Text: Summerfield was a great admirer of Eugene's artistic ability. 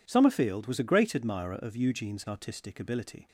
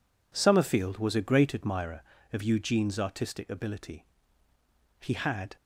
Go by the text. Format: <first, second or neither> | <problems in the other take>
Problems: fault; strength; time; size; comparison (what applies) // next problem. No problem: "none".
first | goes on to say "He had"; from 4.9 s on; 0.58 s long